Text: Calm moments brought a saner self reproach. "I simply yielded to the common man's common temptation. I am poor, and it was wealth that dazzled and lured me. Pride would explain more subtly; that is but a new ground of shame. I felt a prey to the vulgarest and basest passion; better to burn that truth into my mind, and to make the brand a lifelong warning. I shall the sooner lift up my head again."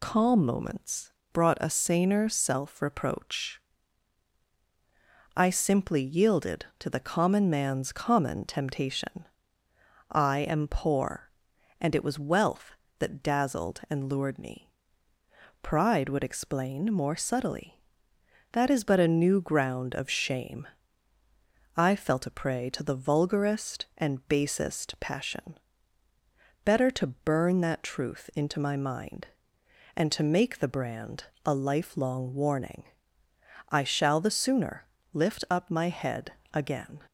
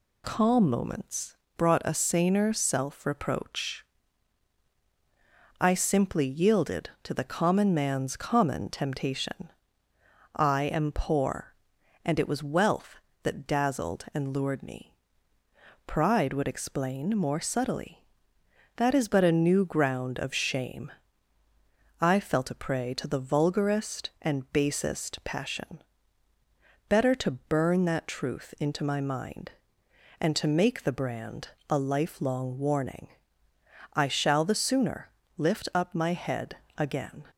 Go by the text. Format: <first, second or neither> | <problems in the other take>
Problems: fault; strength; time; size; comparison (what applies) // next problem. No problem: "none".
second | loses the start of "Calm"; at 0.0 s; 20 ms // pauses between "moments" and "brought"; slight; at 1.1 s; 0.18 s long; slight in the second // pauses between "brand" and "a"; slight; at 31.2 s; 0.20 s long; slight in the second // pauses between "sooner" and "lift"; slight; at 34.8 s; 0.26 s long; slight in the second // pauses between "head" and "again"; slight; at 36.3 s; 0.20 s long; slight in the second